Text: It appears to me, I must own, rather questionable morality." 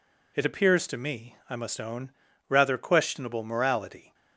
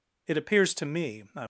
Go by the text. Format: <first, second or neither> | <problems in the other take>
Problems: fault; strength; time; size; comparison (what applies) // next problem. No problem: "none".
first | stops before "must own rather questionable morality"; at 1.4 s